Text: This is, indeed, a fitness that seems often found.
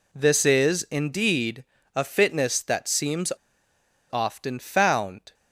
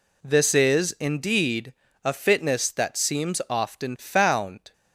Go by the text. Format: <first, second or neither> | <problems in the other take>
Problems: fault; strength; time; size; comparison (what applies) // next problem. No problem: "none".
second | pauses between "seems" and "often"; noticeable; at 3.3 s; 0.80 s long